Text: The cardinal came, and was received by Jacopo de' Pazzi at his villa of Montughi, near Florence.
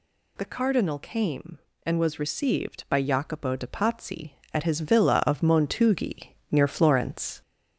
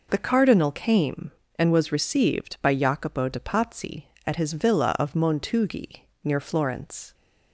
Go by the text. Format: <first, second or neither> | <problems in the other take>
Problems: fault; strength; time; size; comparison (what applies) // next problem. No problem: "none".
second | gets louder; slight; throughout; 2.5 dB